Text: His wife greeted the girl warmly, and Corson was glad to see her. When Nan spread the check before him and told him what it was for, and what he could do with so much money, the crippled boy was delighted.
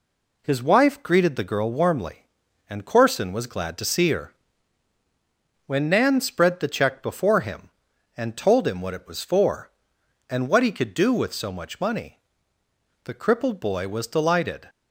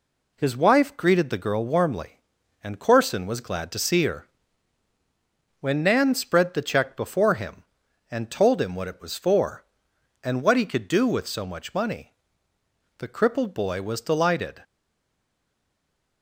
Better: first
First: none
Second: stays silent after the last word; noticeable; from 14.6 s on; 1.6 s long

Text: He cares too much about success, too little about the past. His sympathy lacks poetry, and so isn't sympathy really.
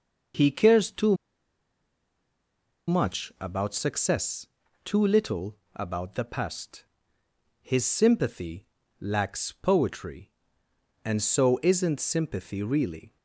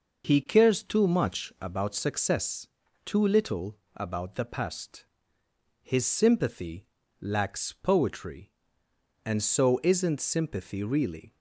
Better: second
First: pauses between "too" and "much"; strong; at 1.1 s; 1.7 s long // pauses between "little" and "about"; slight; at 5.5 s; 0.18 s long // pauses between "sympathy" and "lacks"; slight; at 8.6 s; 0.36 s long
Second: pauses between "little" and "about"; slight; at 3.7 s; 0.18 s long // pauses between "sympathy" and "lacks"; slight; at 6.8 s; 0.36 s long

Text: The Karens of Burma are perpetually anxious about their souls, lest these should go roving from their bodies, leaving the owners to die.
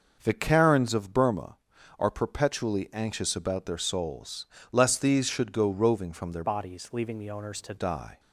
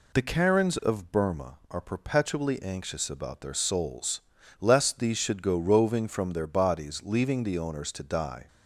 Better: second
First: starts louder than the rest; noticeable; until 1.2 s; 6 dB // changes voice from "bodies" to "to"; from 6.4 to 7.7 s; 1.3 s long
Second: none

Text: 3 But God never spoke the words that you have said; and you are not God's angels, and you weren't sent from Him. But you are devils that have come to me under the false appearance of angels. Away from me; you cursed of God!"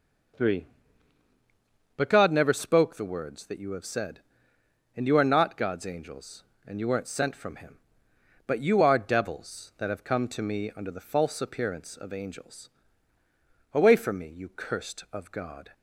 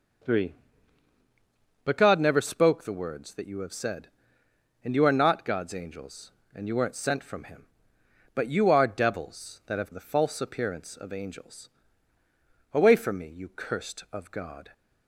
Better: first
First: none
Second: skips "come to me under"; at 9.9 s

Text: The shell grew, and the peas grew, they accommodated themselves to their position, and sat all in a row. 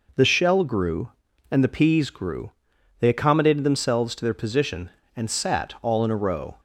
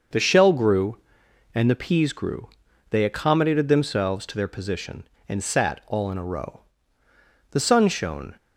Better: first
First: none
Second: starts louder than the rest; noticeable; until 1.6 s; 6 dB // goes on to say "The sun shone"; noticeable; from 7.4 s on; 0.86 s long

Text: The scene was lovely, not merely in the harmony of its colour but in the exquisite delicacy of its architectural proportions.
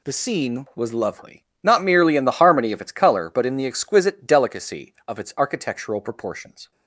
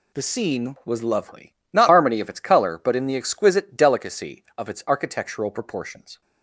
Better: first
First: none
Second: skips "merely in the"; at 1.8 s

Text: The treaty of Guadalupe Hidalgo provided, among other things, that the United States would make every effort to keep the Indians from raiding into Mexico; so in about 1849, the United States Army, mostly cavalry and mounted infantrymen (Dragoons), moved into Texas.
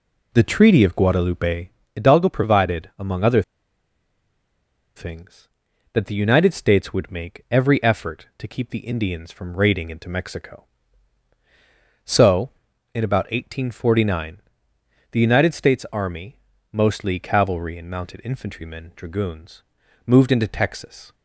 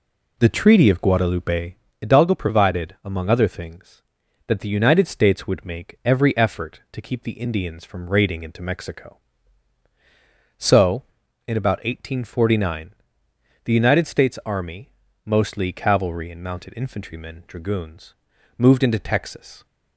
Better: second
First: pauses between "Guadalupe" and "Hidalgo"; slight; at 1.6 s; 0.24 s long // pauses between "other" and "things"; strong; at 3.4 s; 1.5 s long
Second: pauses between "Guadalupe" and "Hidalgo"; slight; at 1.7 s; 0.24 s long

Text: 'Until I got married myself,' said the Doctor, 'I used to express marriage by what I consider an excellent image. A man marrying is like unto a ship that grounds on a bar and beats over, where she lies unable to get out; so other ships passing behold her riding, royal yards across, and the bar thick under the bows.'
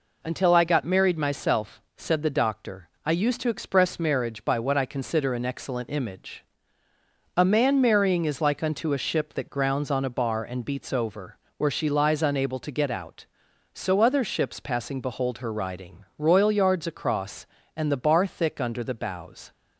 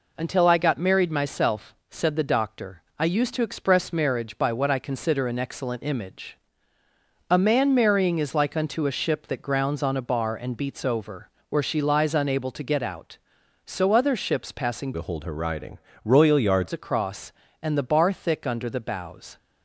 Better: first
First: none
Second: changes voice from "behold" to "yards"; from 14.9 to 16.7 s; 1.8 s long

